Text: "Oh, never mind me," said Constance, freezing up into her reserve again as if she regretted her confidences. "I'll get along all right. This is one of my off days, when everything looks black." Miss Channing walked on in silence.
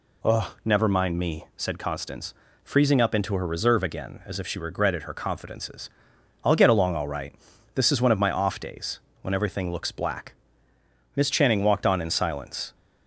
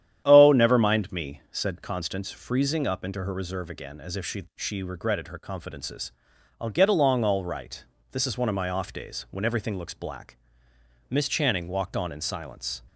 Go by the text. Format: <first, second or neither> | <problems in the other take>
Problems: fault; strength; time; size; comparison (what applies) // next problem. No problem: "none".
first | starts louder than the rest; strong; until 1.2 s; 10 dB // says "she" twice; at 4.5 s